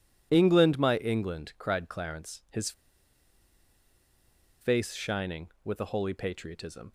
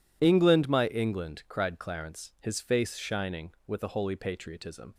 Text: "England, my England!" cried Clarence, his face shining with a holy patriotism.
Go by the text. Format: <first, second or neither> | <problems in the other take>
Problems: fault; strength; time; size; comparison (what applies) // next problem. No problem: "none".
second | pauses between "his" and "face"; strong; at 2.7 s; 1.8 s long